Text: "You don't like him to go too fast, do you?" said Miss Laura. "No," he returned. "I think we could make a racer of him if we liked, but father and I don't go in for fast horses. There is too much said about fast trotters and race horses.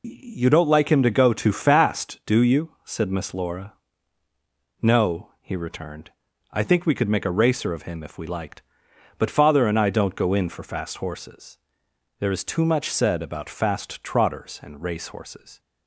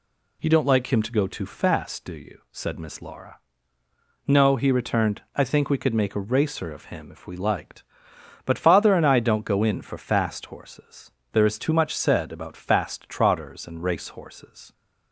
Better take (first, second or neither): neither